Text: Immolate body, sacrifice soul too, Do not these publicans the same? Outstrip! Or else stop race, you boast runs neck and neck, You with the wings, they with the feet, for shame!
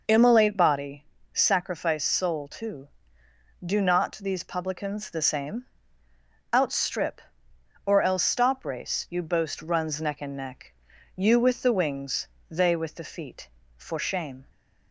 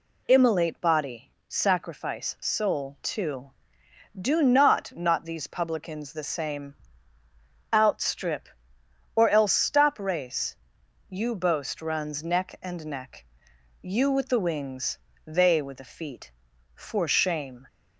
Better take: first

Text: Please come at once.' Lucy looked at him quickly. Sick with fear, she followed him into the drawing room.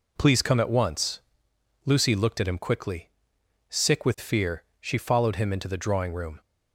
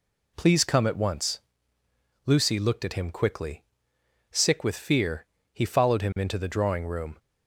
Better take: first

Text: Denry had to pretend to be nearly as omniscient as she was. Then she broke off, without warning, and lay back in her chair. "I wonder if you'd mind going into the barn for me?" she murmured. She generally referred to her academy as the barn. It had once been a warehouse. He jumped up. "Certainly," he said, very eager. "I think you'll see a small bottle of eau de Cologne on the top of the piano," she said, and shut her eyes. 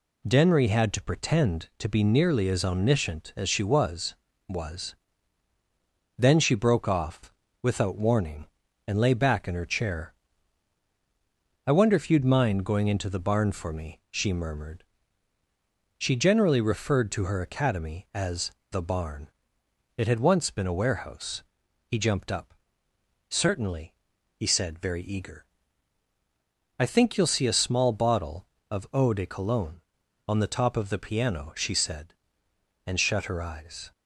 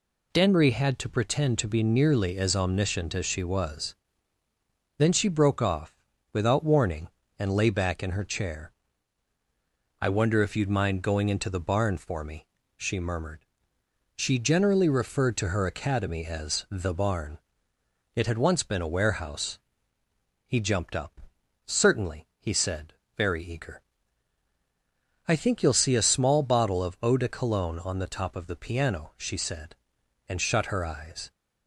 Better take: second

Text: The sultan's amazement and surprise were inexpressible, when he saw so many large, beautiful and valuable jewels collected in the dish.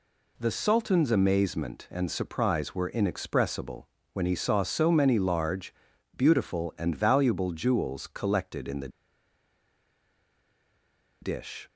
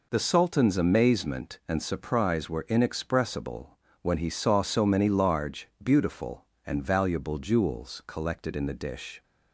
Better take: second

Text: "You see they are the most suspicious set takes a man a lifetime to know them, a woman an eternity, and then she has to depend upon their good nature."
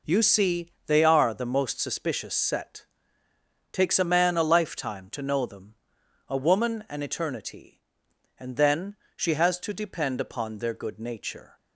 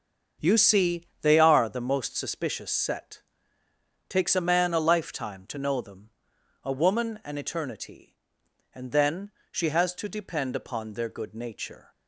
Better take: first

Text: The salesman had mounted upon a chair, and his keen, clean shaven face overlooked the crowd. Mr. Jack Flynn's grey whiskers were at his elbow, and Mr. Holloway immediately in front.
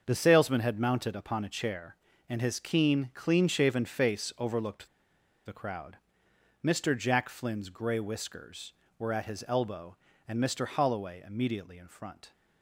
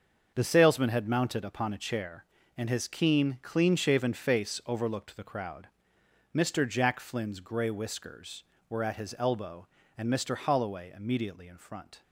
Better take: second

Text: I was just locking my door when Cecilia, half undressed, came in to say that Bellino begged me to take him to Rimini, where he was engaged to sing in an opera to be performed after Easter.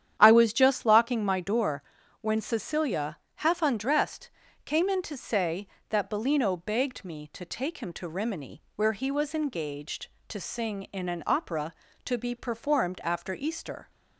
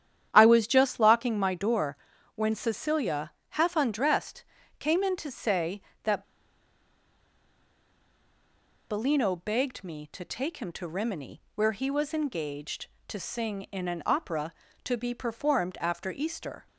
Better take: first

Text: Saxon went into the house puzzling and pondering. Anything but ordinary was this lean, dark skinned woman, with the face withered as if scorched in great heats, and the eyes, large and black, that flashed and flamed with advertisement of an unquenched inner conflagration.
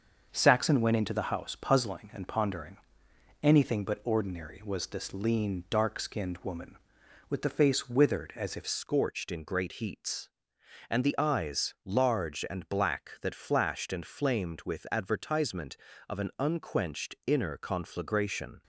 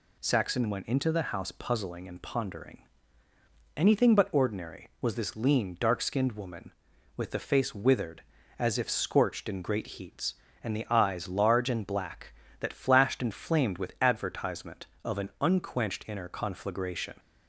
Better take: second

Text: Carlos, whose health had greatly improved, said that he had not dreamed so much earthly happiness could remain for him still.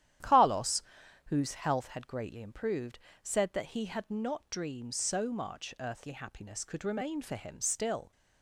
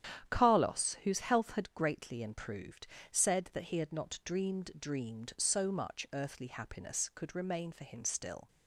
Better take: first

